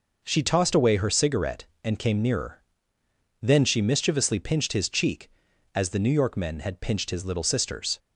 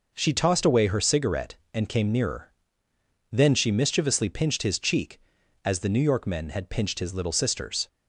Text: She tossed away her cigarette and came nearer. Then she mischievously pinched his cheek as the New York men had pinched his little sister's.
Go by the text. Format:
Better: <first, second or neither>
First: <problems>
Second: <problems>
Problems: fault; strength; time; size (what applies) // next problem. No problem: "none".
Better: neither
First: none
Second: none